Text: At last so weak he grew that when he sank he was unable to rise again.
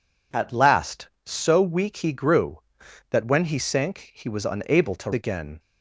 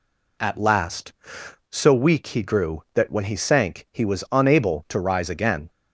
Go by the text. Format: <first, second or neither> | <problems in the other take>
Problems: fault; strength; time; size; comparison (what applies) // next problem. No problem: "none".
second | skips "rise"; at 5.1 s